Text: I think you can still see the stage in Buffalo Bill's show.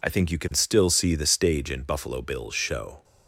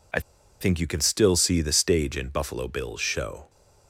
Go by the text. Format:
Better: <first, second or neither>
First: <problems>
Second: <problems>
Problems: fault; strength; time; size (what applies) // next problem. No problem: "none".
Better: first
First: none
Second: pauses between "I" and "think"; at 0.1 s; 0.41 s long